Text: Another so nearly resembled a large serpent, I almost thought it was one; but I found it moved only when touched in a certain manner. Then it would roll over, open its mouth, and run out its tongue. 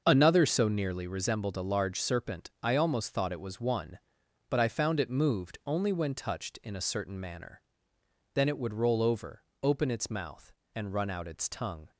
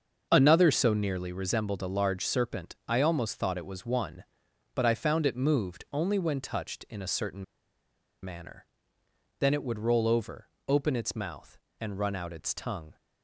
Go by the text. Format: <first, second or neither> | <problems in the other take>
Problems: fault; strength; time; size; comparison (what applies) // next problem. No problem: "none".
first | starts louder than the rest; until 1.3 s; 6.5 dB; also in the first // pauses between "certain" and "manner"; noticeable; at 7.4 s; 0.79 s long